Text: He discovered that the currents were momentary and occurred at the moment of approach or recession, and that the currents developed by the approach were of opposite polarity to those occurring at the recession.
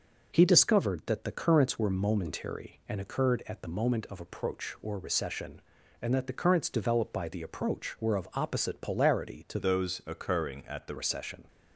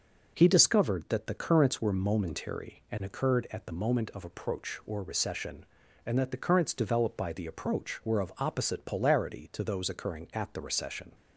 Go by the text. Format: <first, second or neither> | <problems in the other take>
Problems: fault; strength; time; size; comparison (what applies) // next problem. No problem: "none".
second | changes voice from "those" to "the"; from 9.5 to 10.9 s; 1.4 s long